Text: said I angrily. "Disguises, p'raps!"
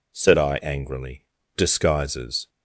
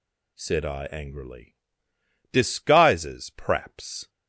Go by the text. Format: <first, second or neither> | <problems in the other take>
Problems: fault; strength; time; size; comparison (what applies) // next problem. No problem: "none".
second | stops before "p'raps"; at 2.4 s